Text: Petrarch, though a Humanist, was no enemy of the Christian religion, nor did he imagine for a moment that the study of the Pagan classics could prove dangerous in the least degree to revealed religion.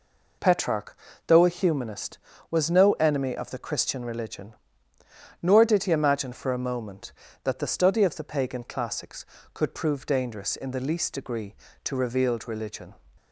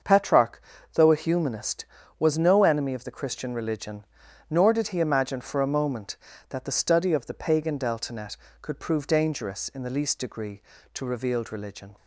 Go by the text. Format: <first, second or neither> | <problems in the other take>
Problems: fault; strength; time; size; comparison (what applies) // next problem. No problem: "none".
first | starts louder than the rest; until 1.3 s; 6.5 dB // says "deltanet" for "classics"; at 7.7 s